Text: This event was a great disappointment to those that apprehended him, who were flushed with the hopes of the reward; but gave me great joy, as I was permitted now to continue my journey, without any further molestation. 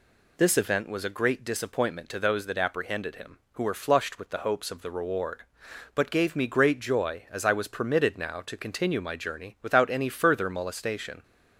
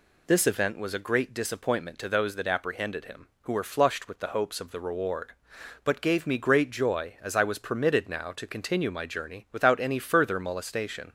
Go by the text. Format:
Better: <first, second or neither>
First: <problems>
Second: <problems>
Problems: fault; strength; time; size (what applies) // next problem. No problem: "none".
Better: neither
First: none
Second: none